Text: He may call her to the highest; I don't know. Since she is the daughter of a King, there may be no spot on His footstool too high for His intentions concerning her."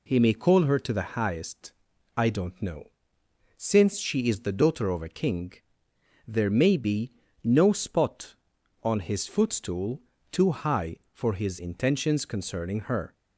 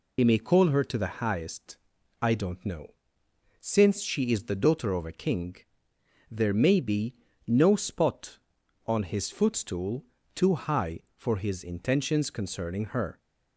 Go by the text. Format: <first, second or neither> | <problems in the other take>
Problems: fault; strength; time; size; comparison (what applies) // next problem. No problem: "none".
first | loses the start of "He"; at 0.1 s; 65 ms // pauses between "be" and "no"; slight; at 7.1 s; 0.32 s long; slight in the first // pauses between "footstool" and "too"; slight; at 10.0 s; 0.30 s long; slight in the first